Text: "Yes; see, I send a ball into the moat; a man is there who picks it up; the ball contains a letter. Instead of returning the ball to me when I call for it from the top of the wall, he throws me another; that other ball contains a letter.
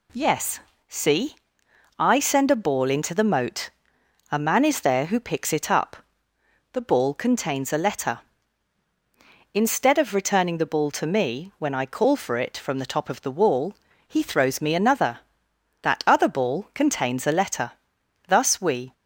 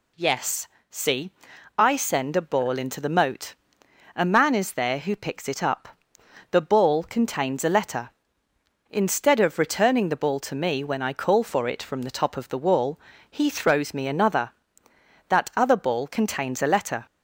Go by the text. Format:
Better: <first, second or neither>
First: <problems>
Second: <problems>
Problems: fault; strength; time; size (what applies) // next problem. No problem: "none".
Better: second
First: goes on to say "Thus we"; noticeable; from 18.2 s on; 0.66 s long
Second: none